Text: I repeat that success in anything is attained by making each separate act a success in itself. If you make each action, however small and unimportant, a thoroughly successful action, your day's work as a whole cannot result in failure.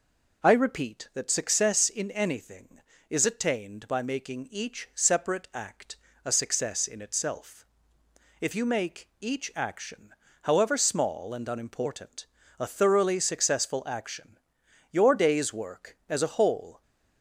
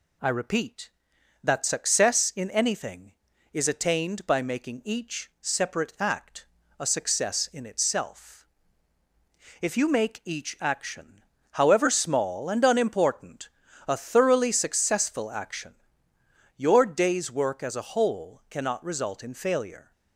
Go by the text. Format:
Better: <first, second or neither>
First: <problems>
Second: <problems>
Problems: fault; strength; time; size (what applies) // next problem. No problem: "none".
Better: second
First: pauses between "act" and "a"; slight; at 5.9 s; 0.26 s long // stops before "cannot result in failure"; at 16.8 s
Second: pauses between "act" and "a"; slight; at 6.4 s; 0.34 s long